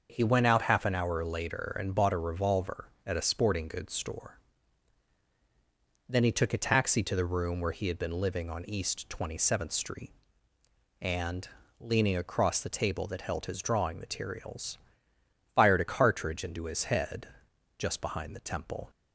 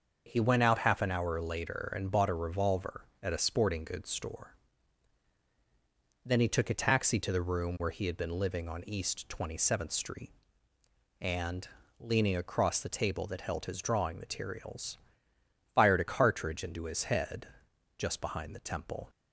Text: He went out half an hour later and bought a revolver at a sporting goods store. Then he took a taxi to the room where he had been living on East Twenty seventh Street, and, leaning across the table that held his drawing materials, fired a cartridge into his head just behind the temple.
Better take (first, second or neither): neither